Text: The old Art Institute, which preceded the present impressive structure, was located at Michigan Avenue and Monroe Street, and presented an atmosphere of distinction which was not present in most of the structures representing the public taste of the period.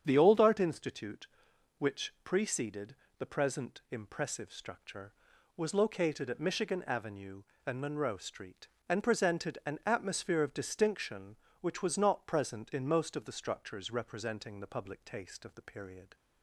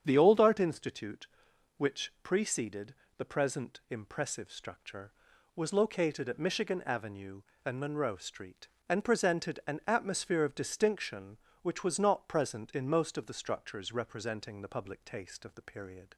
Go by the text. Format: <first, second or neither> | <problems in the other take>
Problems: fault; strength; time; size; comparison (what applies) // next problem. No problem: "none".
neither | starts louder than the rest; strong; the same in both // pauses between "preceded" and "the"; slight; the same in both